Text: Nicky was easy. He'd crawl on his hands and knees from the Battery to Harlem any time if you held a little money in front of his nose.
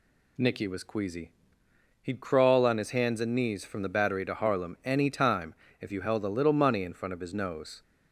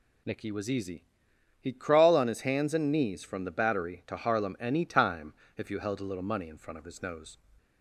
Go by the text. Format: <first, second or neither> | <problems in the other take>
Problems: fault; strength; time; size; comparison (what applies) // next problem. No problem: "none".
second | says "queasy" for "easy"; at 0.8 s // pauses between "time" and "if"; slight; at 5.5 s; 0.26 s long; slight in the second